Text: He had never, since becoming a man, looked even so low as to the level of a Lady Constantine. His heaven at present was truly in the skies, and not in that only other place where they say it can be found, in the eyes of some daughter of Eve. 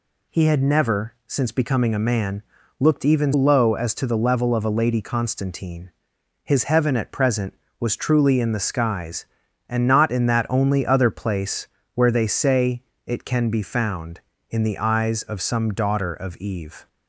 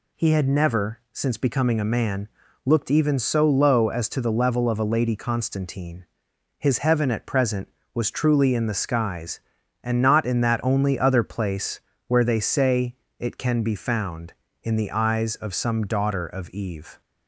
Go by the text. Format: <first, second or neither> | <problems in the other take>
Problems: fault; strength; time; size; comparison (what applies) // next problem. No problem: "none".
second | skips "so"; at 3.3 s // pauses between "place" and "where"; slight; at 11.6 s; 0.26 s long; slight in the second // pauses between "say" and "it"; slight; at 12.8 s; 0.24 s long; slight in the second